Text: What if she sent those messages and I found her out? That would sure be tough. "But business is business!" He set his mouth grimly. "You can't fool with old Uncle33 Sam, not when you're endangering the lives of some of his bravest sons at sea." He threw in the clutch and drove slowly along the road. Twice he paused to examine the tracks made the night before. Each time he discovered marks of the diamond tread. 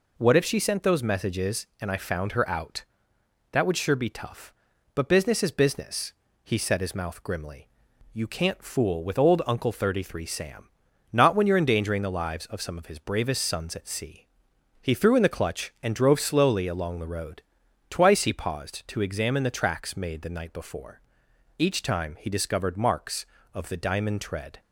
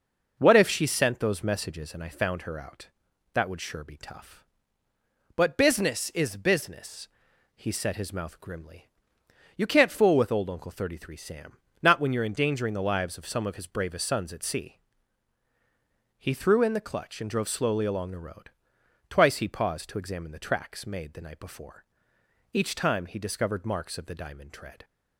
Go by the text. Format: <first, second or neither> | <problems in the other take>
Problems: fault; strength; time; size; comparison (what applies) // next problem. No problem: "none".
neither | none